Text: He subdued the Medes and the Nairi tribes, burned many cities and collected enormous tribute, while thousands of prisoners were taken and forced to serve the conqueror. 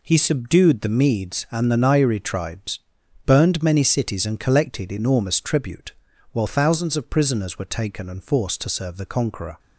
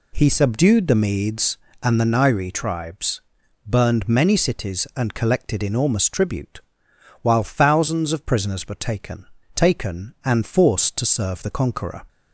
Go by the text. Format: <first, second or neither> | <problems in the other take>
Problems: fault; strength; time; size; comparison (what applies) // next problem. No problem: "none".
first | says "taken" twice; at 9.5 s